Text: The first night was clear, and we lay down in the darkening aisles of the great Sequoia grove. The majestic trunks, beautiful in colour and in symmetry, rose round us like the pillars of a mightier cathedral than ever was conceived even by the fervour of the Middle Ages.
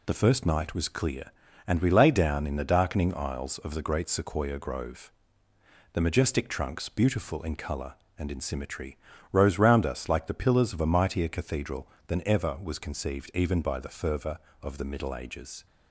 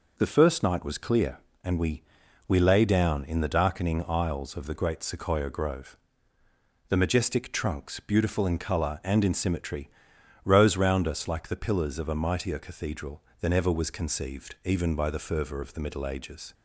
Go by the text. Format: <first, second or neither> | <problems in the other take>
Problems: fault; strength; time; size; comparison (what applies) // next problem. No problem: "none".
first | says "we" twice; at 2.4 s